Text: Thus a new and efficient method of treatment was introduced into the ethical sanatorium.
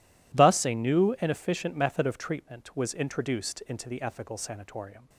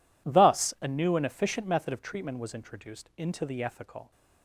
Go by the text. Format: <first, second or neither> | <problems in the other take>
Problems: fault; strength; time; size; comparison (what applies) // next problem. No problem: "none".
first | stops before "sanatorium"; at 4.1 s